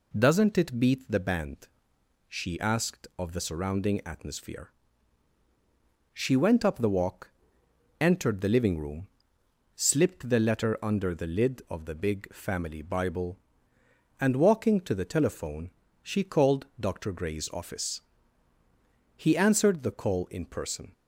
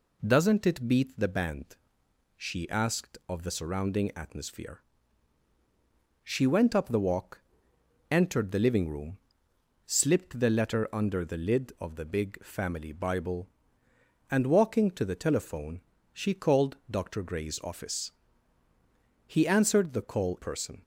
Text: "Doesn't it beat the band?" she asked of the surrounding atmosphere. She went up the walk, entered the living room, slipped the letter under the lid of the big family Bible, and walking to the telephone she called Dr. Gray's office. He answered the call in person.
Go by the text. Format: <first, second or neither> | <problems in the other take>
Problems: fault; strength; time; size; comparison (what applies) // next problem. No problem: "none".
first | pauses between "telephone" and "she"; slight; at 15.8 s; 0.32 s long; slight in the first // skips "in"; at 20.3 s